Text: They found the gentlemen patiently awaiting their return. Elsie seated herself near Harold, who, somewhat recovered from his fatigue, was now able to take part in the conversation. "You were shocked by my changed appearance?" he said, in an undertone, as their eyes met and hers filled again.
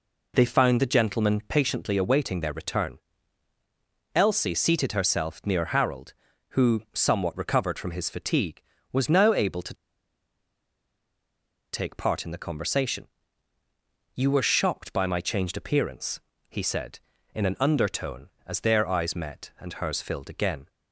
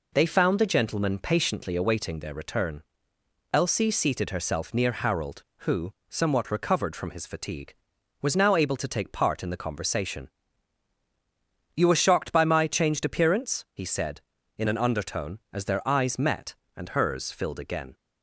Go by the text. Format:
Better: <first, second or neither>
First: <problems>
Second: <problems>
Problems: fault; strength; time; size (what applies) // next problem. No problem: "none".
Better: second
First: pauses between "to" and "take"; strong; at 9.7 s; 1.9 s long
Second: none